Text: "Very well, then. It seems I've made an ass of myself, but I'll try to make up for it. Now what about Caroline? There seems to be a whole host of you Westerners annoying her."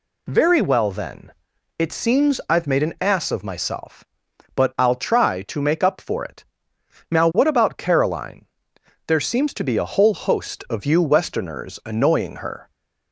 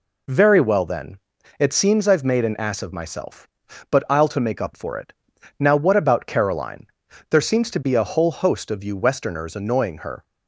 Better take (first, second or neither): first